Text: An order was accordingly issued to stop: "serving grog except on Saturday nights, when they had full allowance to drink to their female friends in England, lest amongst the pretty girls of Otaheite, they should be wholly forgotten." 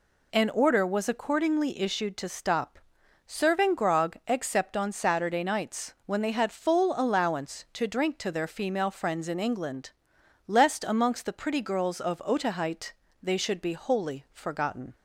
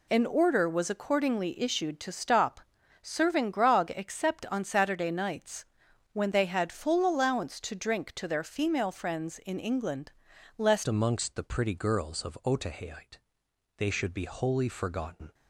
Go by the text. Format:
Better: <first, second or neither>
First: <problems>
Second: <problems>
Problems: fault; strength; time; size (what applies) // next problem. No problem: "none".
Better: first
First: none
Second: changes voice at "amongst"; from 10.8 s on; 4.5 s long